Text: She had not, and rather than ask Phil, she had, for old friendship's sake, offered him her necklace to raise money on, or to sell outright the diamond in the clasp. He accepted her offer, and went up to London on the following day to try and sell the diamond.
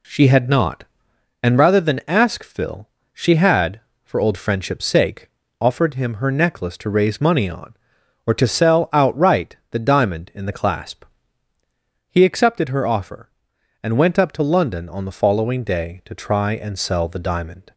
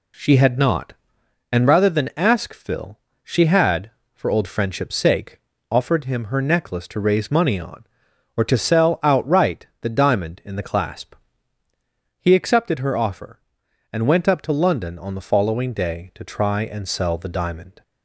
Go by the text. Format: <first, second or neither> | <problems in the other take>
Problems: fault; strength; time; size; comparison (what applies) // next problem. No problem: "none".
neither | none